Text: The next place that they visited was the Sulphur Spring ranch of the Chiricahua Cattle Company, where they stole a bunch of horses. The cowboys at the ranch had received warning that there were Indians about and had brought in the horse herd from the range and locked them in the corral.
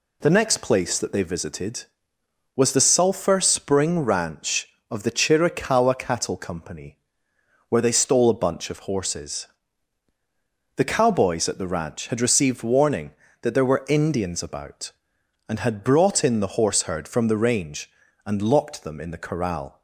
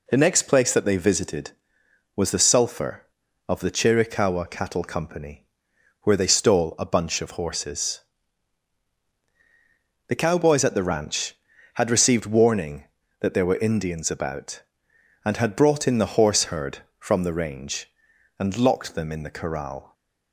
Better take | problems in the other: first | skips "Spring ranch"; at 3.2 s

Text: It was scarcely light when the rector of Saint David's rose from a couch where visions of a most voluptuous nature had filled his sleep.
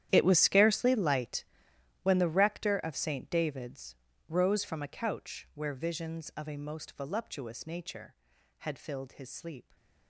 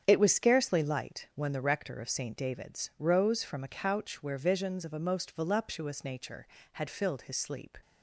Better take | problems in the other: second | gets quieter; strong; throughout; 17.5 dB // starts louder than the rest; strong; until 1.1 s; 11 dB; strong in the second // pauses between "light" and "when"; noticeable; at 1.4 s; 0.58 s long // pauses between "David's" and "rose"; slight; at 3.9 s; 0.34 s long

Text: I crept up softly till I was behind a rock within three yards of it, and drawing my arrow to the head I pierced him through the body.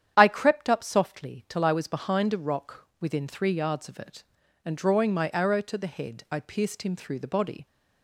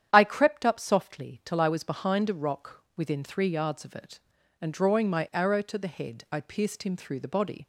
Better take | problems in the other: neither | starts louder than the rest; strong; the same in both

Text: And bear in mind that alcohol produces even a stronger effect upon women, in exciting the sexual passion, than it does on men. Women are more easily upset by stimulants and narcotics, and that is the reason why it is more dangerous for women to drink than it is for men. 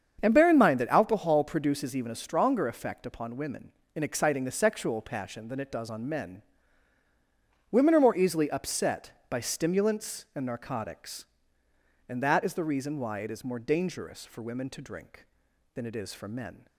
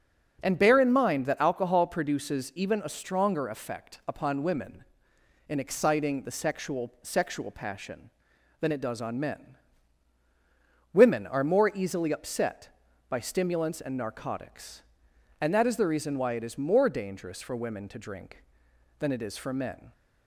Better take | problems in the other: first | starts louder than the rest; until 1.4 s; 6.5 dB; strong in the first // says "sexual" twice; at 7.0 s

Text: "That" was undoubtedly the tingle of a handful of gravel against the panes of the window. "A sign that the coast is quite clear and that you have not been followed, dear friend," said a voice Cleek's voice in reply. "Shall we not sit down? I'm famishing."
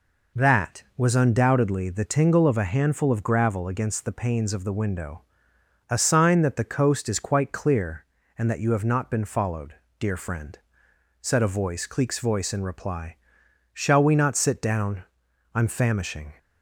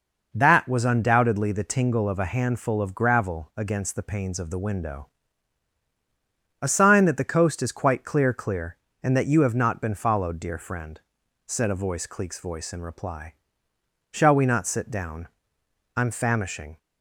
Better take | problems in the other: first | says "clear" twice; at 8.3 s

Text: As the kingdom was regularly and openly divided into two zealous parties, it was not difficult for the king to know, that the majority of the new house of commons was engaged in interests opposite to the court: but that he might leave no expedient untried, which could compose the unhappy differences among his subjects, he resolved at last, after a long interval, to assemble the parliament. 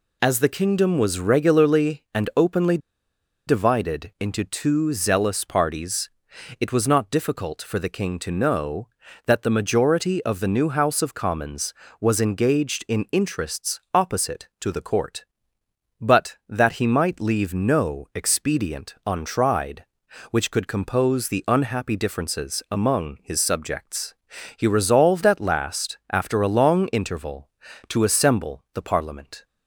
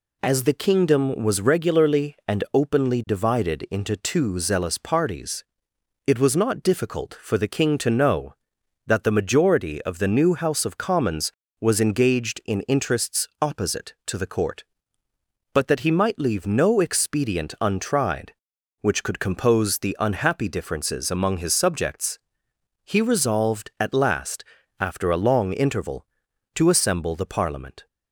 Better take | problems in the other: second | pauses between "openly" and "divided"; noticeable; at 2.7 s; 0.69 s long

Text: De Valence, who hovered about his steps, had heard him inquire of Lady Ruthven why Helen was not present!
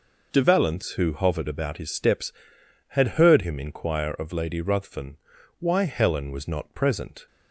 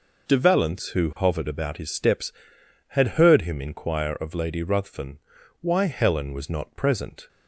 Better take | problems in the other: neither | pauses between "Ruthven" and "why"; the same in both

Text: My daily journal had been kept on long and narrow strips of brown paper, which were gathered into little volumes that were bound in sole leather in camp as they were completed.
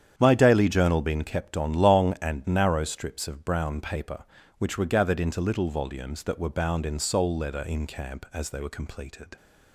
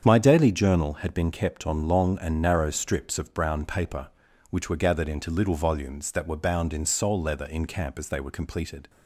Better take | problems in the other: second | starts louder than the rest; strong; until 1.1 s; 9 dB; strong in the second // skips "had"; at 1.0 s

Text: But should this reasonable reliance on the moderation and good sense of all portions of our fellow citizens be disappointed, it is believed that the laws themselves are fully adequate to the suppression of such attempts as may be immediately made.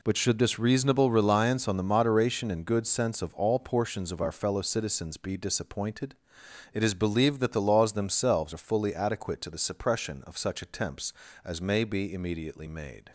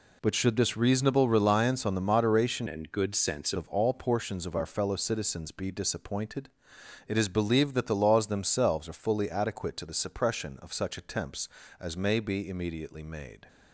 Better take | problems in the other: first | changes voice from "and" to "sense"; from 2.6 to 3.5 s; 0.9 s long

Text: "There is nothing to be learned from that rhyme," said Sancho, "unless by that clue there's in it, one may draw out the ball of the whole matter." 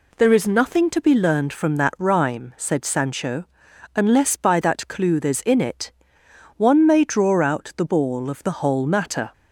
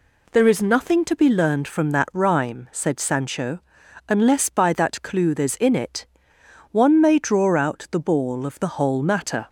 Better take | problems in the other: neither | none

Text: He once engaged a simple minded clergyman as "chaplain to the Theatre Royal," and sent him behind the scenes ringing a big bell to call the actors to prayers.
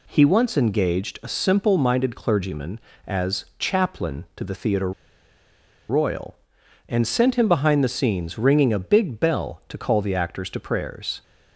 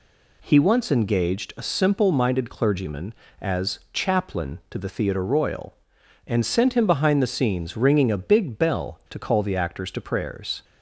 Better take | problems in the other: second | pauses between "Theatre" and "Royal"; at 4.9 s; 0.98 s long

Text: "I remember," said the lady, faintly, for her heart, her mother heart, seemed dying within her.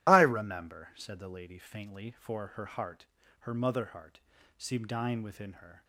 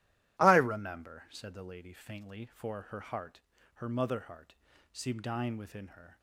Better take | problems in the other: second | loses the start of "I"; at 0.0 s; 30 ms

